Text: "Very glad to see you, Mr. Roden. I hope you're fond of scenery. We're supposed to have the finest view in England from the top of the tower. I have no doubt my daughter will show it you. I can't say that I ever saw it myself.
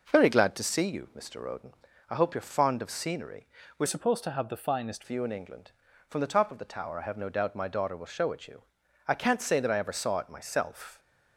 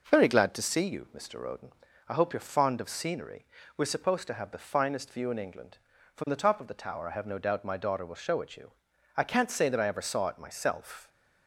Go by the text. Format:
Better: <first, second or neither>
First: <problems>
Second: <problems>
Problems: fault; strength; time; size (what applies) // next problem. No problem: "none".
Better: second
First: changes voice from "supposed" to "finest"; from 3.8 to 5.0 s; 1.2 s long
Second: none